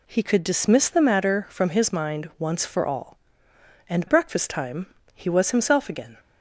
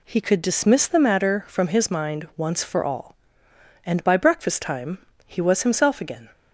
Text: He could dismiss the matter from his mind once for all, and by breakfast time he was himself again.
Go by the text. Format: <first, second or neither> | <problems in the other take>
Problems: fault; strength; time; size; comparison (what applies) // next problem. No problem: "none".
second | skips "by"; at 4.0 s // pauses between "time" and "he"; slight; at 4.8 s; 0.28 s long; slight in the second